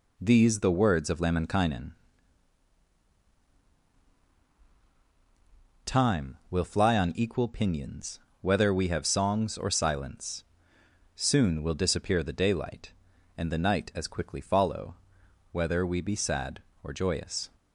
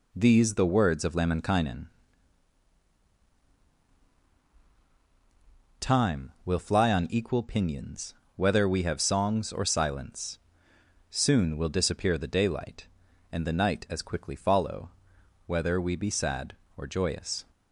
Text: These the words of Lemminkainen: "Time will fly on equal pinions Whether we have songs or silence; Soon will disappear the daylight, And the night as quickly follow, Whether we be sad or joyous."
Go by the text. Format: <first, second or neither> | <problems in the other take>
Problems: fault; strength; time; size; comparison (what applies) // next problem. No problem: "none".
neither | pauses between "pinions" and "Whether"; slight; the same in both